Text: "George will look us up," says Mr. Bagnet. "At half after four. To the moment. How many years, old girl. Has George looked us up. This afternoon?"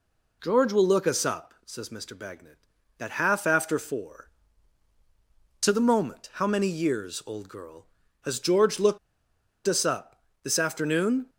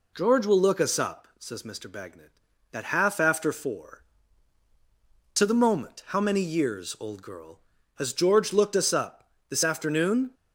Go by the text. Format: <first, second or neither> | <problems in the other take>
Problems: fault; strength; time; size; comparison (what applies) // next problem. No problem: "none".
second | pauses between "looked" and "us"; noticeable; at 8.9 s; 0.68 s long